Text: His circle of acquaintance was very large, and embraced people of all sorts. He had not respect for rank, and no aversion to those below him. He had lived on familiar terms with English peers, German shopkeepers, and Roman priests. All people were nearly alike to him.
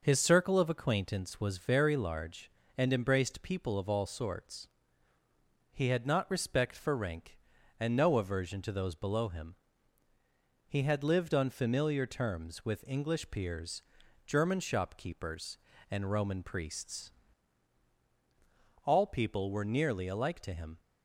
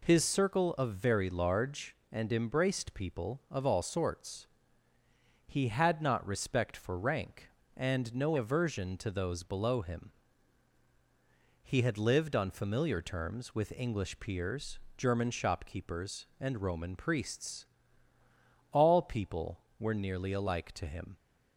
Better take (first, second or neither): first